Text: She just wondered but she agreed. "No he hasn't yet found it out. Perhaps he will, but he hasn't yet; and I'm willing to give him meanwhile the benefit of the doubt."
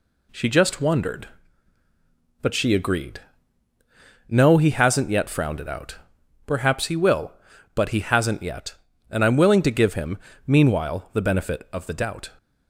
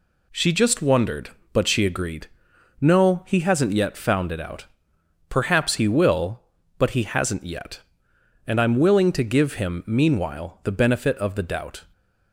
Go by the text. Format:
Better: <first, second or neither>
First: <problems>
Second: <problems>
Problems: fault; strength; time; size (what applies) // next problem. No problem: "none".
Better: second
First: says "frowned" for "found"; at 5.2 s // pauses between "him" and "meanwhile"; slight; at 10.1 s; 0.30 s long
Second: none